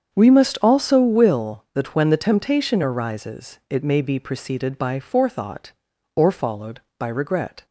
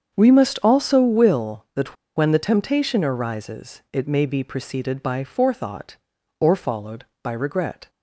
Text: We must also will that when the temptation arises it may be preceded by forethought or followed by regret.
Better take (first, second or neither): first